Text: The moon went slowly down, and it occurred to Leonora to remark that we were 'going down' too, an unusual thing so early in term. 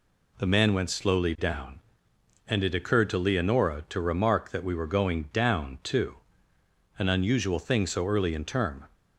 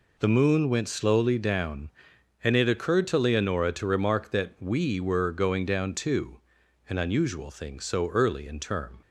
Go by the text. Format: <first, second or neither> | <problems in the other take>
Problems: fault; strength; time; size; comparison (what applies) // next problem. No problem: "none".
second | says "man" for "moon"; at 0.4 s